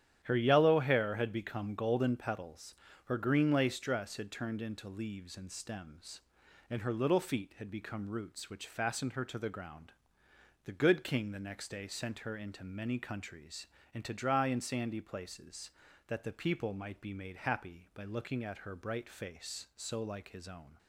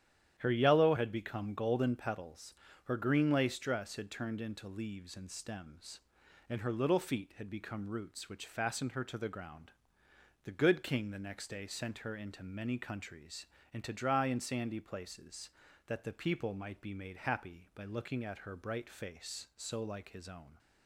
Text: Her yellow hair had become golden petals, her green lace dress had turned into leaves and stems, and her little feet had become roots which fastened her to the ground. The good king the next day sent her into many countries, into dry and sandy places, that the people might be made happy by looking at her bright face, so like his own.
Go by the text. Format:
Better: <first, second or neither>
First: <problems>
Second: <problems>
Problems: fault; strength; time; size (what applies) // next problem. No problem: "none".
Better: first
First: starts louder than the rest; strong; until 1.2 s; 10 dB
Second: starts louder than the rest; strong; until 1.4 s; 10.5 dB // skips "hair"; at 0.9 s